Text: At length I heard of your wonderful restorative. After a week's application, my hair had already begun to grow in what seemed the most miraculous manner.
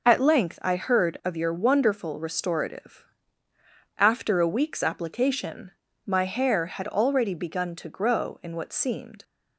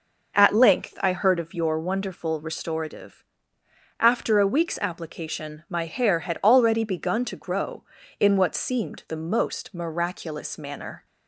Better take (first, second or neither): second